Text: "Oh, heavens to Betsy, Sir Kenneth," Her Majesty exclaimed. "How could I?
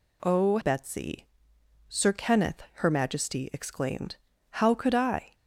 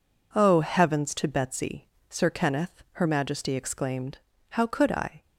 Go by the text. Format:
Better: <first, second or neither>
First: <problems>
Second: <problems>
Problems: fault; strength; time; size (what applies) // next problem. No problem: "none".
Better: second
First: skips "heavens to"; at 0.6 s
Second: none